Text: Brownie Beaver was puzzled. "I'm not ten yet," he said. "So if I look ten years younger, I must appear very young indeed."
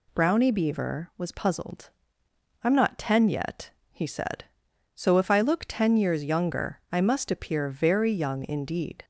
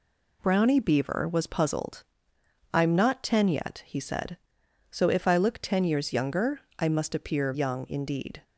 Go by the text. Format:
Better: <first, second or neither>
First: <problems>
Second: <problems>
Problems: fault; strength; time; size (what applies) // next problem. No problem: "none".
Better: first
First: none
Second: skips "very"; at 7.5 s